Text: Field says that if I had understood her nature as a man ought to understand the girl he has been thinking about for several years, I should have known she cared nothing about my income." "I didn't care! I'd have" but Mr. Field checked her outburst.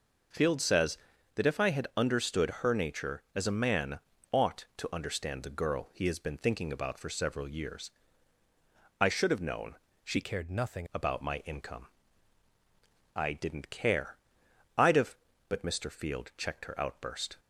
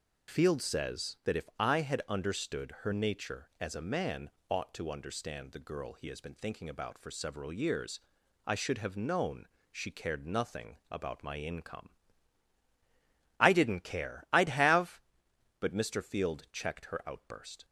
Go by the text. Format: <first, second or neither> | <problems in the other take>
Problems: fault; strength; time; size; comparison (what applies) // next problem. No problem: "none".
second | pauses between "man" and "ought"; slight; at 3.9 s; 0.32 s long; slight in the second // pauses between "known" and "she"; slight; at 9.7 s; 0.28 s long; slight in the second // changes voice from "cared" to "nothing"; from 10.2 to 10.8 s; 0.6 s long